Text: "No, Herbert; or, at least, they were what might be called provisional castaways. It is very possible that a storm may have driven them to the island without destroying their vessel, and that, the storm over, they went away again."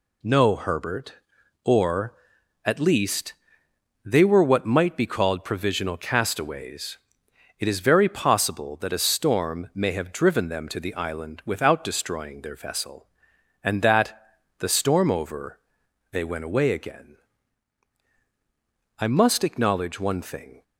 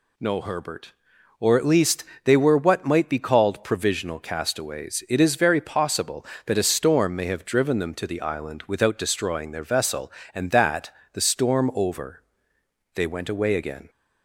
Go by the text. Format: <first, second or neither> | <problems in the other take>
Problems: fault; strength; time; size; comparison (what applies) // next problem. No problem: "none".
second | goes on to say "I must acknowledge one thing"; from 18.9 s on; 1.6 s long